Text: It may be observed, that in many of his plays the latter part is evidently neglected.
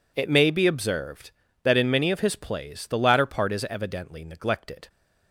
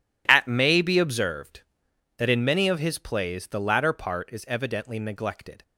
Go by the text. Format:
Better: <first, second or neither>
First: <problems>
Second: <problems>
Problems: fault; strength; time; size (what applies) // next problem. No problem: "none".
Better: first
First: none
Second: says "At" for "It"; at 0.2 s